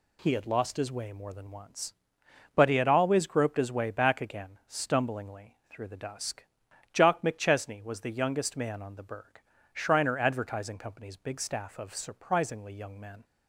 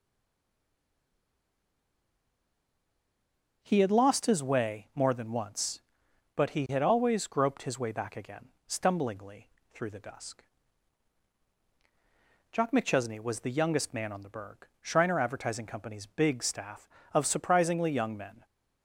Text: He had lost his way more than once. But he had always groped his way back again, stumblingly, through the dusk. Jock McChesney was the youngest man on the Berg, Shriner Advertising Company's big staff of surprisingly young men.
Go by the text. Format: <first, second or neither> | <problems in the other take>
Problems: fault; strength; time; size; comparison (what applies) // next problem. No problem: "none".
first | stays silent before the first word; strong; until 3.6 s; 3.6 s long // starts louder than the rest; until 4.6 s; 6.5 dB